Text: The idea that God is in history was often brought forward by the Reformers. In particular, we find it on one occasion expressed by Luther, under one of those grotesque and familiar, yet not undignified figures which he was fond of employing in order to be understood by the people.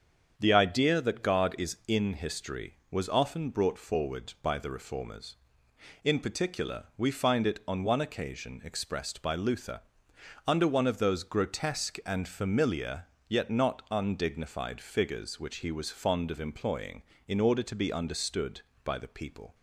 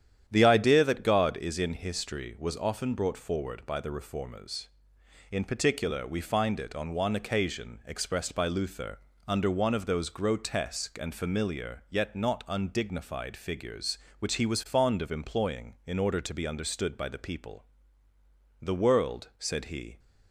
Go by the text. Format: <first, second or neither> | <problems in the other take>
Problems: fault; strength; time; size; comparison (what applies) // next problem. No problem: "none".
first | starts louder than the rest; strong; until 1.2 s; 9.5 dB; strong in the first // goes on to say "The world said he"; from 18.6 s on; 1.3 s long